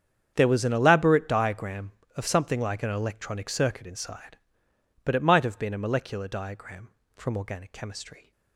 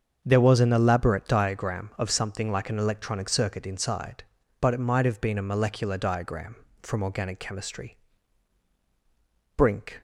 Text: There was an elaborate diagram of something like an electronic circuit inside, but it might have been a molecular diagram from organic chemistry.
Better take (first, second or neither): first